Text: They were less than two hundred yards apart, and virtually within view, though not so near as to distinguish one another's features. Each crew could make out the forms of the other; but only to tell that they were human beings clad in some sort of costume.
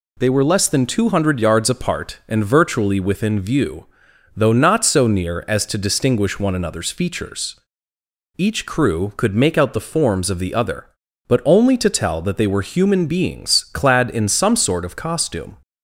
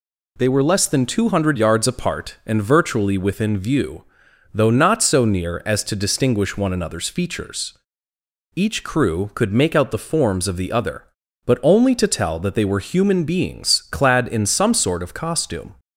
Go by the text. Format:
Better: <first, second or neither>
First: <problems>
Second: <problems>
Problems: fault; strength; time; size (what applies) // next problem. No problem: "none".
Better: neither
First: none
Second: none